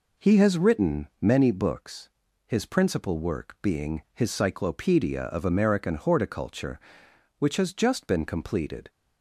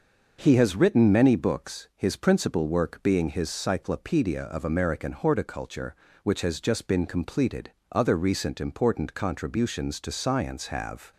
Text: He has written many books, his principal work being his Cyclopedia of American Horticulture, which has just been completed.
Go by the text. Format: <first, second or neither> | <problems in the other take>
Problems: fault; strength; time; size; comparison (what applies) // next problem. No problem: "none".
first | goes on to say "Other recent important contributions to science have"; strong; from 7.9 s on; 3.2 s long